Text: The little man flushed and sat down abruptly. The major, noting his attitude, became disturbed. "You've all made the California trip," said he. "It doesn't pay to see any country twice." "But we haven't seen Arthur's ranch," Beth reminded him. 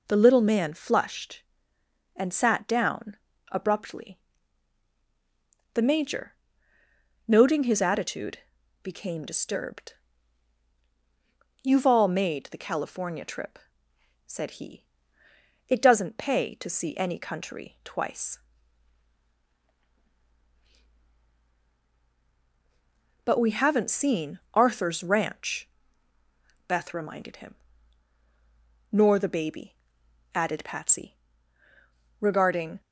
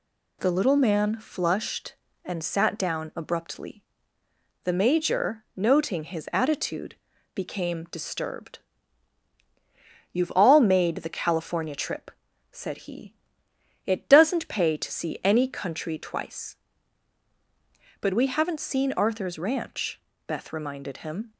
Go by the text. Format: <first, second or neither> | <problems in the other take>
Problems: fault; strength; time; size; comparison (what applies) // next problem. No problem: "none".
second | pauses between "down" and "abruptly"; slight; at 3.1 s; 0.34 s long // pauses between "seen" and "Arthur's"; slight; at 24.3 s; 0.16 s long // goes on to say "Nor the baby added Patsy regarding"; strong; from 28.9 s on; 3.8 s long